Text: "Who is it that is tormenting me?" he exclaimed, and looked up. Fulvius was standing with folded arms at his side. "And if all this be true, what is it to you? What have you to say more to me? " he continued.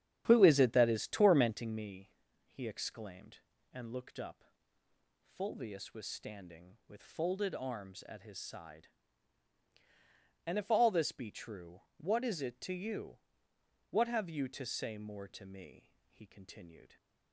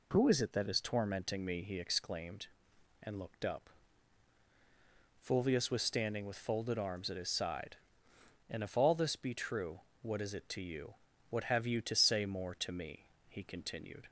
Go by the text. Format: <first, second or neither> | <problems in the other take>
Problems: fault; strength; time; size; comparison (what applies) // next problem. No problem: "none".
second | starts louder than the rest; strong; until 1.8 s; 9.5 dB